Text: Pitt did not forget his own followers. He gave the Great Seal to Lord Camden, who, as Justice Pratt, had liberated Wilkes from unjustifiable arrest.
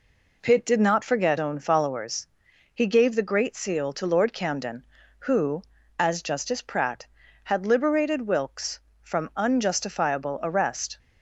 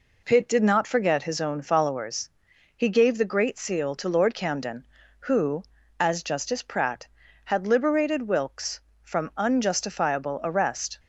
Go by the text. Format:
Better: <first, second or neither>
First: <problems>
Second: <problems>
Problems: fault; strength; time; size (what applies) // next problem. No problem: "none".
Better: second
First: skips "his"; at 1.3 s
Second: none